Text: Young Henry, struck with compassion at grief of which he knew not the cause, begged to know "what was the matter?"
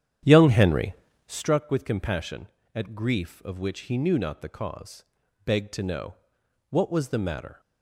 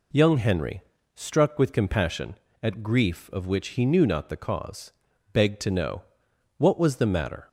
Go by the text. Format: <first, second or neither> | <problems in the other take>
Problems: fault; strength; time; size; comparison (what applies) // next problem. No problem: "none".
second | starts louder than the rest; strong; until 1.6 s; 10 dB // pauses between "know" and "what"; noticeable; at 6.1 s; 0.56 s long; noticeable in the second